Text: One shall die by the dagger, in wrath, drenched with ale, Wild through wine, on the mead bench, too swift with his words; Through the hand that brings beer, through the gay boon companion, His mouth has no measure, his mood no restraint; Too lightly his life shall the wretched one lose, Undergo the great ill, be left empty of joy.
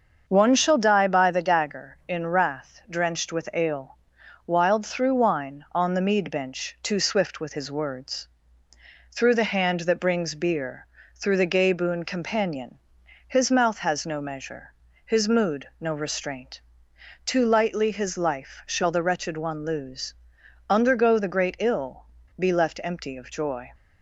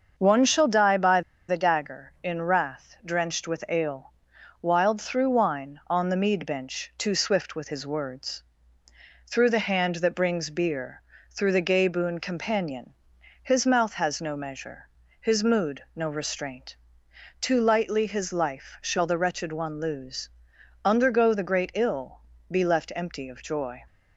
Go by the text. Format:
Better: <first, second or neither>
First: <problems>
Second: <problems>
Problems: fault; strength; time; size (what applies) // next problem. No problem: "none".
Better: first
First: starts louder than the rest; until 1.2 s; 6.5 dB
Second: starts louder than the rest; until 1.1 s; 6.5 dB // pauses between "by" and "the"; slight; at 1.2 s; 0.28 s long